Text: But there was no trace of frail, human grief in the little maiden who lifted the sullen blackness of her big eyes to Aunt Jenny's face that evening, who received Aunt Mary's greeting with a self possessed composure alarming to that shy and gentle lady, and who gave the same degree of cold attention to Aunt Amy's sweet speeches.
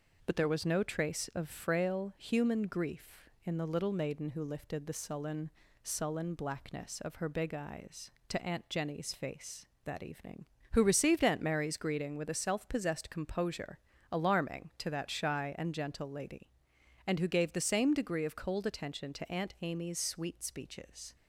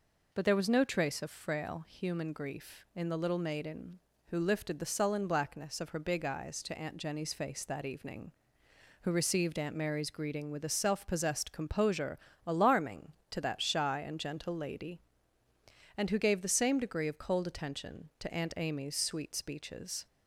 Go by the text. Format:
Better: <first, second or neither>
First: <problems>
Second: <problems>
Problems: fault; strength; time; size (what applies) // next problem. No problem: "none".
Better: second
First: says "sullen" twice; at 5.8 s // pauses between "composure" and "alarming"; slight; at 13.7 s; 0.32 s long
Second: pauses between "composure" and "alarming"; slight; at 12.1 s; 0.28 s long